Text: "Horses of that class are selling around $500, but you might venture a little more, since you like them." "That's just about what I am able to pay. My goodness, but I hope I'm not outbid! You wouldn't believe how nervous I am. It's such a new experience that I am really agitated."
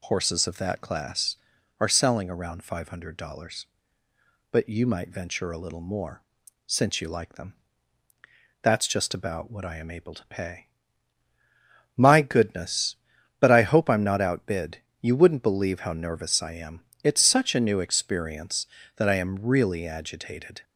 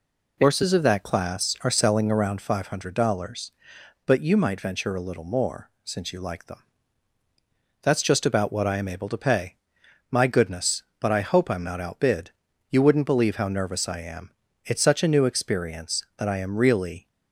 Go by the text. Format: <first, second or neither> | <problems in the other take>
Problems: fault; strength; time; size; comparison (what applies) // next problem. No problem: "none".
first | stops before "agitated"; at 17.0 s